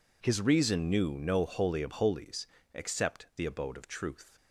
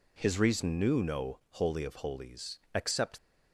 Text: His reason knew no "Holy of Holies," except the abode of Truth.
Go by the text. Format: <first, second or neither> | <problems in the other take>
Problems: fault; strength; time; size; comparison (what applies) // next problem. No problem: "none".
first | stops before "the abode of Truth"; at 3.1 s